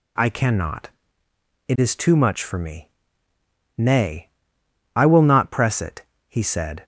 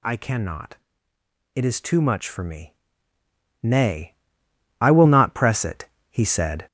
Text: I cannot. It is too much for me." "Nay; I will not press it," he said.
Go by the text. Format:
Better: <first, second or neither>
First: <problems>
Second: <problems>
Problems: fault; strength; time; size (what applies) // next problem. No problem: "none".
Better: first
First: none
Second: gets louder; noticeable; throughout; 5.5 dB